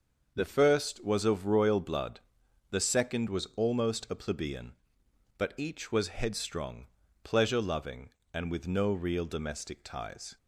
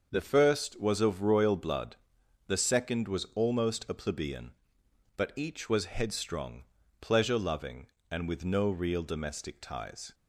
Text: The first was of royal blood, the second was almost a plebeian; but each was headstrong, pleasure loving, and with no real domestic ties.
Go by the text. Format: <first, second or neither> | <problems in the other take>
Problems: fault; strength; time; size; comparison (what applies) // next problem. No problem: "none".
neither | starts louder than the rest; the same in both